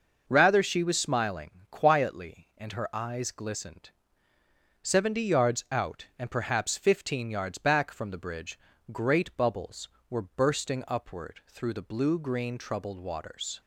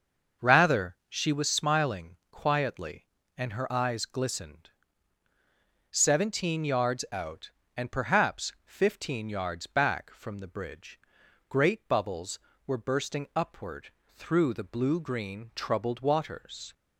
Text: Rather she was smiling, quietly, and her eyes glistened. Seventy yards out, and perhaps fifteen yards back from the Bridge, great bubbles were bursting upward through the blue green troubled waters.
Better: first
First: none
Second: starts louder than the rest; until 1.5 s; 6 dB // says "Seventeen" for "Seventy"; at 5.9 s // pauses between "upward" and "through"; slight; at 13.9 s; 0.16 s long

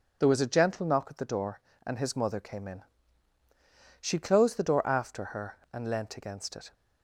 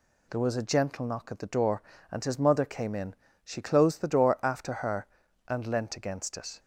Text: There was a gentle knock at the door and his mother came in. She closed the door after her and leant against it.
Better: neither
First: none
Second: none

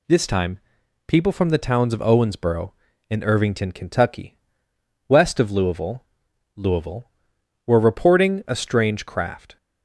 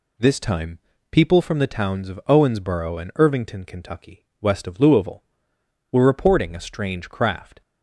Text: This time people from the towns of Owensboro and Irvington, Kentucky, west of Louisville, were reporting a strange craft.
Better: second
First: pauses between "time" and "people"; noticeable; at 0.5 s; 0.48 s long // says "Louisville" twice; at 6.5 s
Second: pauses between "time" and "people"; slight; at 0.7 s; 0.32 s long

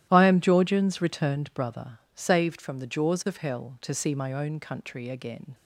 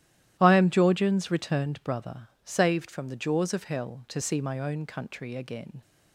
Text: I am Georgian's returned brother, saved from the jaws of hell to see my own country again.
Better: neither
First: starts louder than the rest; strong; until 1.1 s; 13 dB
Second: starts louder than the rest; strong; until 1.4 s; 13 dB

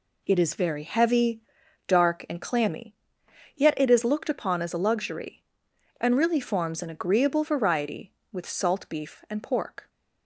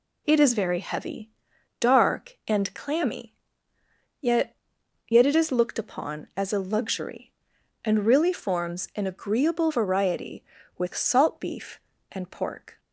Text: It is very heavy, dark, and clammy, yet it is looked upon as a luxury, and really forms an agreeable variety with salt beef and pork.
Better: first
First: none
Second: says "yet" twice; at 5.0 s

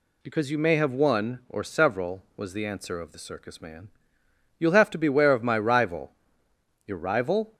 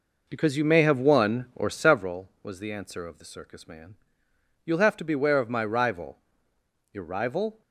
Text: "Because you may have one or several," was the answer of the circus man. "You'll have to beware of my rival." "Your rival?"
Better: first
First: none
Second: starts louder than the rest; noticeable; until 2.2 s; 4.5 dB

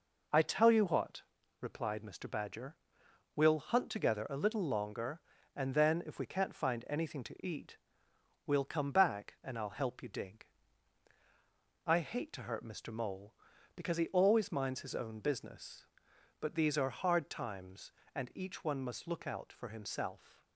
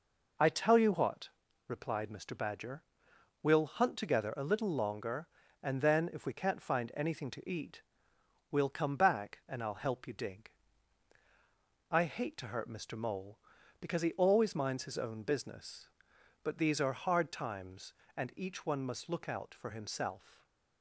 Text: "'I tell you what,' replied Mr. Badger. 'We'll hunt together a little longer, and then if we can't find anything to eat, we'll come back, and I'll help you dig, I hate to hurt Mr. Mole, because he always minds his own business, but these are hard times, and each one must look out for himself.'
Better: neither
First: none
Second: none

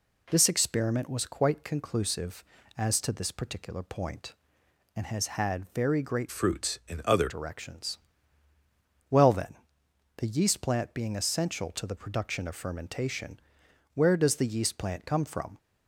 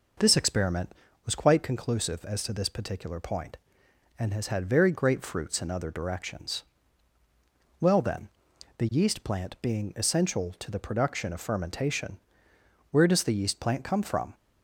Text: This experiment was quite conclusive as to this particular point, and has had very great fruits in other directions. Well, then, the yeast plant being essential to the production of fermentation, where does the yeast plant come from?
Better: second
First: changes voice from "fruits" to "other"; from 6.3 to 7.2 s; 0.9 s long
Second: none

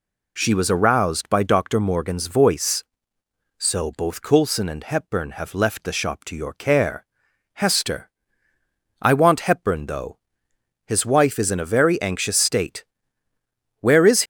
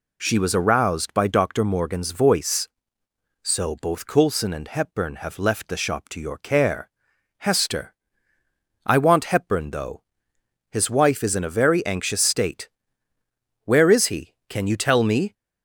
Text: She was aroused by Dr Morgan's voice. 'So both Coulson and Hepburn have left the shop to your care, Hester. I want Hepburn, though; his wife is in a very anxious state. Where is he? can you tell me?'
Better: second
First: stops before "he can you tell me"; at 14.2 s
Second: none

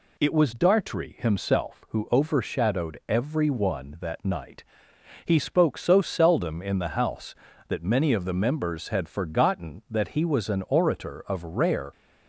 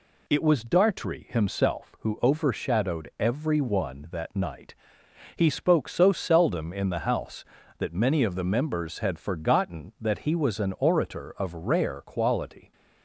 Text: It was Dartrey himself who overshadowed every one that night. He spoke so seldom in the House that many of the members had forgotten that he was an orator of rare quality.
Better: second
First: stops before "quality"; at 11.9 s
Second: none

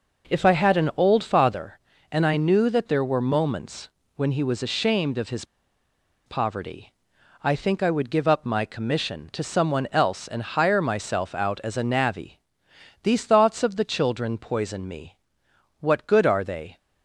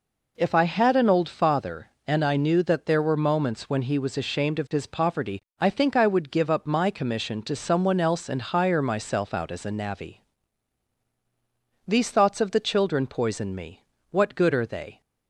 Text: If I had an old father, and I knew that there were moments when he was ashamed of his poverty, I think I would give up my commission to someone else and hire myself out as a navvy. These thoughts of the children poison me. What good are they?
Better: second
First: pauses between "moments" and "when"; slight; at 3.8 s; 0.26 s long // pauses between "his" and "poverty"; noticeable; at 5.4 s; 0.82 s long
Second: none

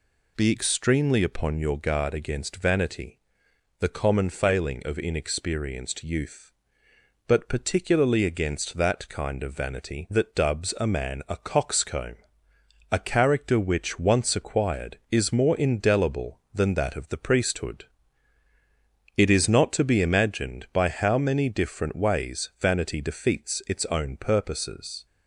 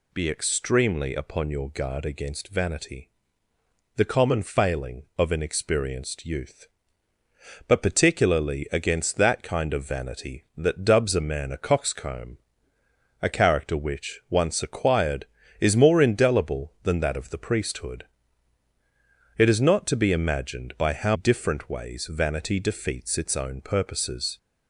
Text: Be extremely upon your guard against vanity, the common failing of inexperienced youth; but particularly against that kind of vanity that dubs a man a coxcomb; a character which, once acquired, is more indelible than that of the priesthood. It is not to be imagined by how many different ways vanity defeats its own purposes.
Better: first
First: none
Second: skips "many"; at 21.1 s

